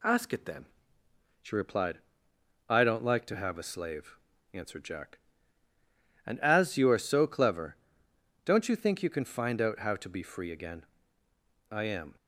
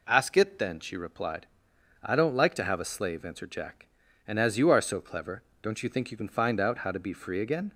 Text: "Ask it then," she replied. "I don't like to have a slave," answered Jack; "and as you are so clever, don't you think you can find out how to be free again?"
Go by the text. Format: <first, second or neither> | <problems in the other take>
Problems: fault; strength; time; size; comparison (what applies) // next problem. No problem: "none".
second | goes on to say "I am"; slight; from 11.6 s on; 0.46 s long